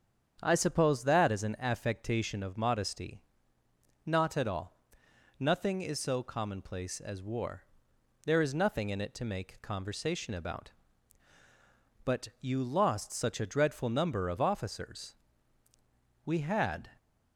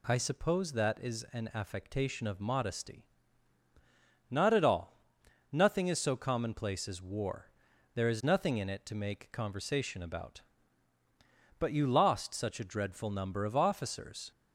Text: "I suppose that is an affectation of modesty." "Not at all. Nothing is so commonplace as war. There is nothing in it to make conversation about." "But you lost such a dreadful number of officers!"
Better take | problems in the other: second | starts louder than the rest; strong; until 1.4 s; 8 dB // goes on to say "We had"; noticeable; from 16.2 s on; 0.68 s long

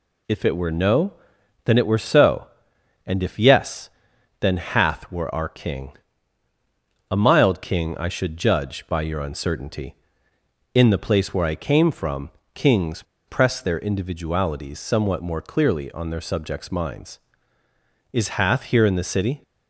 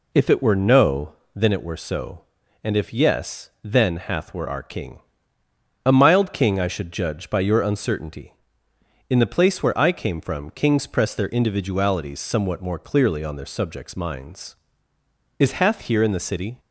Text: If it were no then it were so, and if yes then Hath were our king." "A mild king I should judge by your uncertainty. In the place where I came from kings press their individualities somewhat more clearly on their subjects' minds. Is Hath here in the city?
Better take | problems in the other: second | pauses between "no" and "then"; noticeable; at 1.1 s; 0.52 s long; slight in the second // pauses between "yes" and "then"; noticeable; at 3.8 s; 0.52 s long // pauses between "from" and "kings"; slight; at 12.3 s; 0.24 s long // pauses between "kings" and "press"; slight; at 13.0 s; 0.24 s long

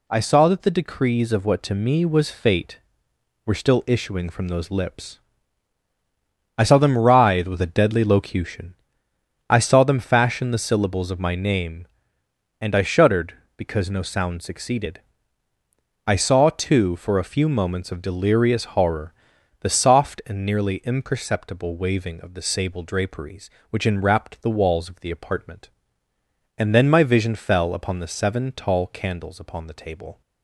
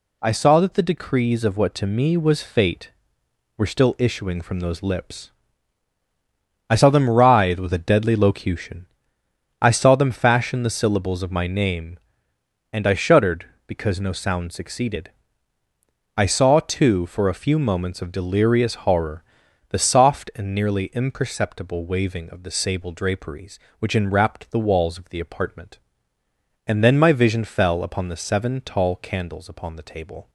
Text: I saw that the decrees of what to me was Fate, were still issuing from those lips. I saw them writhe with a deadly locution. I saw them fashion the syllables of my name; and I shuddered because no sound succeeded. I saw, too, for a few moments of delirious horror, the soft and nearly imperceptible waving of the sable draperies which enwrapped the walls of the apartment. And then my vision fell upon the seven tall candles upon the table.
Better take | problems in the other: neither | none

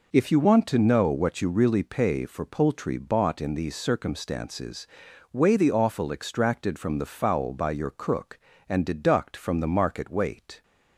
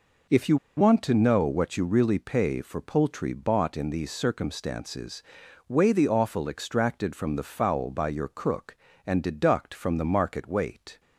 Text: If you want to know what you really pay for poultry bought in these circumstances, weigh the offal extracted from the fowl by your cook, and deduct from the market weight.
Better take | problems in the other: first | pauses between "you" and "want"; slight; at 0.5 s; 0.19 s long

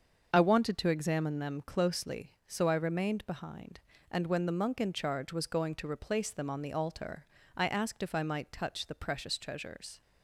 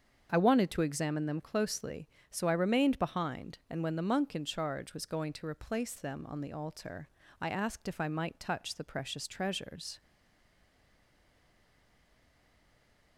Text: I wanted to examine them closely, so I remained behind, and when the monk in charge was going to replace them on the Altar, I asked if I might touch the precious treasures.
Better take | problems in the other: first | starts louder than the rest; until 1.3 s; 7 dB; also in the first // stays silent after the last word; strong; from 10.0 s on; 3.1 s long

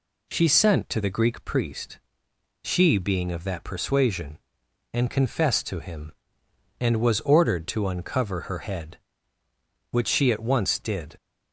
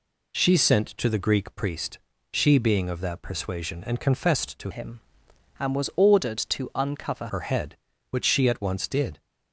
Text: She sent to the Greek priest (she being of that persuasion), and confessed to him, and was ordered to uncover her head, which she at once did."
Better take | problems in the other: first | changes voice from "him" to "uncover"; from 4.7 to 7.2 s; 2.5 s long

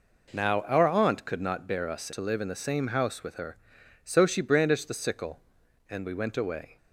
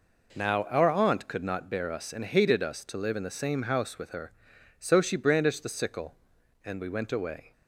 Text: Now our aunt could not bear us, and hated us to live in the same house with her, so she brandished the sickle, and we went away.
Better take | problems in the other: second | skips "and hated us"; at 2.1 s

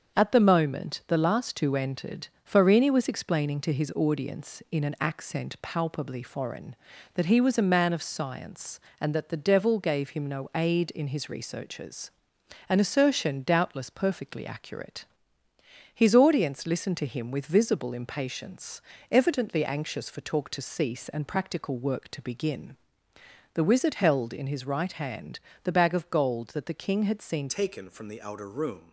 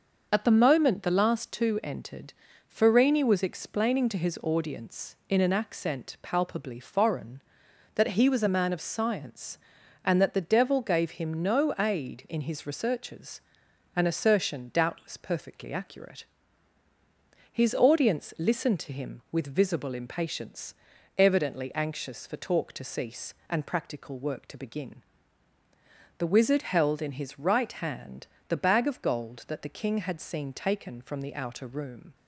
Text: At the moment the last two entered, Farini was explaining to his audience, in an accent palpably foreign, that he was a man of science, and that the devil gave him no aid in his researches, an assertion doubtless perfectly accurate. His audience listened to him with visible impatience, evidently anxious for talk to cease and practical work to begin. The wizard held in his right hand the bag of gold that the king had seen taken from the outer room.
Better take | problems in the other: second | starts louder than the rest; until 1.2 s; 7 dB; also in the second // pauses between "hand" and "the"; slight; at 25.3 s; 0.24 s long; slight in the second // changes voice at "taken"; from 27.4 s on; 1.5 s long

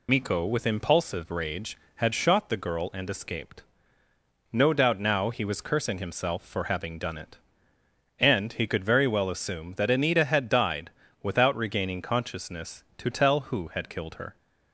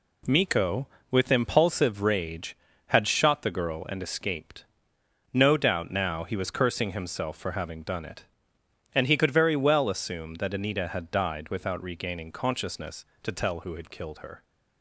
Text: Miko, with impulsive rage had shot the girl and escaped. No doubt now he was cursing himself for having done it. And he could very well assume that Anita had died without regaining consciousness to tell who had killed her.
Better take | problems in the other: second | loses the start of "Miko"; at 0.0 s; 105 ms // pauses between "died" and "without"; slight; at 10.9 s; 0.32 s long

